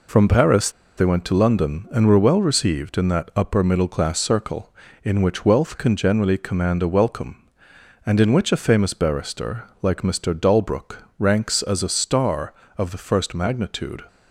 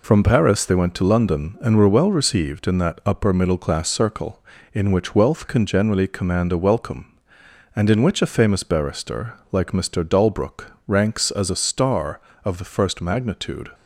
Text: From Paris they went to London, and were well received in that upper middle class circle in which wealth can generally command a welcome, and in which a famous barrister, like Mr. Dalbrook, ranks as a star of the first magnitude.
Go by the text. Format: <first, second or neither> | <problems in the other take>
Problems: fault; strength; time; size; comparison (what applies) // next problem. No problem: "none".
second | pauses between "Paris" and "they"; slight; at 0.7 s; 0.25 s long